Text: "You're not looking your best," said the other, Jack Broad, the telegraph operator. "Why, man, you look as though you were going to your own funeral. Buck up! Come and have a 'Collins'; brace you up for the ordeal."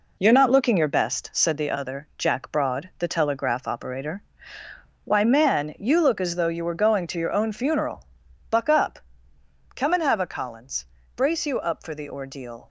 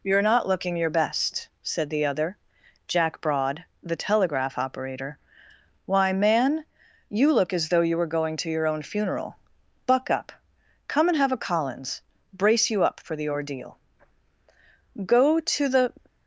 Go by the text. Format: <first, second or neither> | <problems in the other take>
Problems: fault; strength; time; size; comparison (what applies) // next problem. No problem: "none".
first | goes on to say "Go to the"; noticeable; from 15.0 s on; 0.88 s long